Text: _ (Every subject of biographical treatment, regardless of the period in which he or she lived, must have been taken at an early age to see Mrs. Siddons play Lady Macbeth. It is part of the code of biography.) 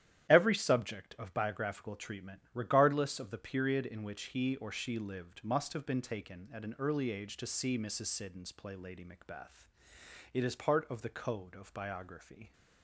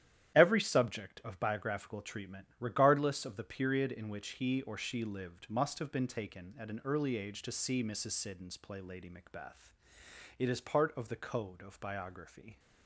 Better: neither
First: starts louder than the rest; strong; until 1.3 s; 11 dB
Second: starts louder than the rest; strong; until 1.4 s; 11 dB

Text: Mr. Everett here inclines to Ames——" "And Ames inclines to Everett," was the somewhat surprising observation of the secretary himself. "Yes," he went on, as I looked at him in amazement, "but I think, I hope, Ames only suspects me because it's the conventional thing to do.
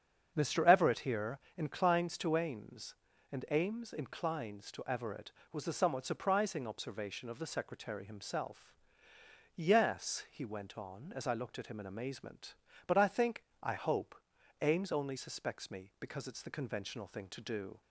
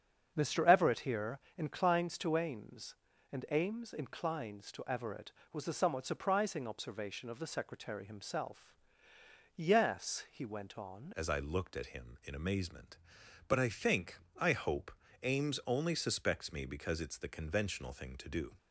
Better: first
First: starts louder than the rest; until 1.3 s; 7 dB // pauses between "here" and "inclines"; slight; at 1.3 s; 0.20 s long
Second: starts louder than the rest; until 1.3 s; 7 dB // pauses between "here" and "inclines"; slight; at 1.3 s; 0.20 s long // changes voice at "as"; from 11.1 s on; 7.4 s long

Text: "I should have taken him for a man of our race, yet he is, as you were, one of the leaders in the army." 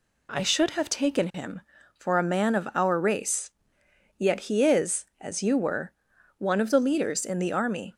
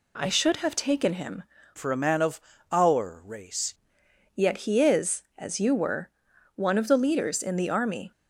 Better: first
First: none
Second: changes voice from "for" to "race"; from 1.7 to 3.7 s; 2.0 s long // pauses between "of" and "our"; slight; at 2.4 s; 0.32 s long

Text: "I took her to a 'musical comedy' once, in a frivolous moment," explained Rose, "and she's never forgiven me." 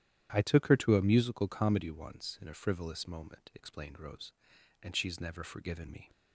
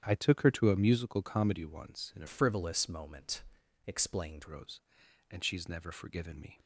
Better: first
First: starts louder than the rest; strong; until 1.3 s; 11 dB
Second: starts louder than the rest; strong; until 1.0 s; 9.5 dB // changes voice from "frivolous" to "explained"; from 2.2 to 4.4 s; 2.2 s long

